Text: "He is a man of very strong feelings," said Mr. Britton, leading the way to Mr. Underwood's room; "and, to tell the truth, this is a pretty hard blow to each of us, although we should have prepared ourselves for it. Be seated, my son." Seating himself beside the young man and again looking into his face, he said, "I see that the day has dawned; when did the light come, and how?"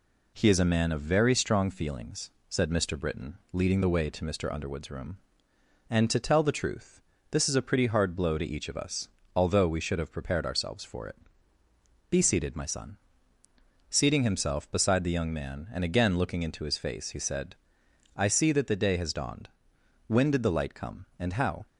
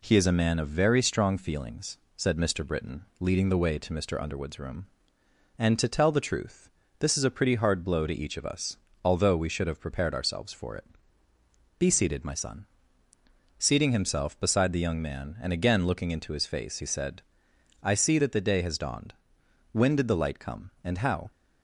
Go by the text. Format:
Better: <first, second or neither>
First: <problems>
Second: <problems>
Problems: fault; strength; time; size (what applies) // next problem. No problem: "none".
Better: neither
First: none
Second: none